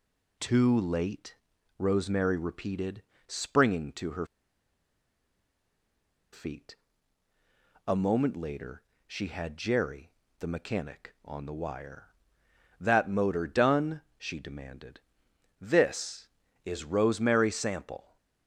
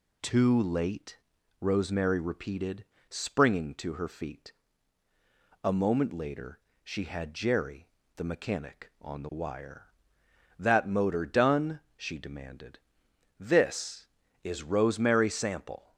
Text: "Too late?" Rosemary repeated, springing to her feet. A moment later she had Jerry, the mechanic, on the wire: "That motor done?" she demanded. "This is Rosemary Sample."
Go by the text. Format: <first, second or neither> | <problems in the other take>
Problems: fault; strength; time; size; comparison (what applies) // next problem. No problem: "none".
second | pauses between "her" and "feet"; strong; at 4.2 s; 2.0 s long // pauses between "later" and "she"; slight; at 8.8 s; 0.24 s long; slight in the second